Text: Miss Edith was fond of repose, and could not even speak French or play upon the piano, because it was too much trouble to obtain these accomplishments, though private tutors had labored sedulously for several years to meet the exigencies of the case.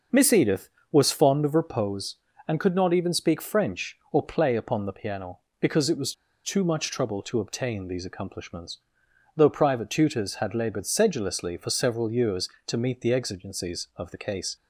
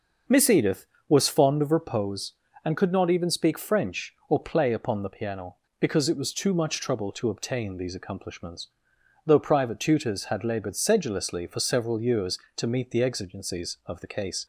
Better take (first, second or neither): second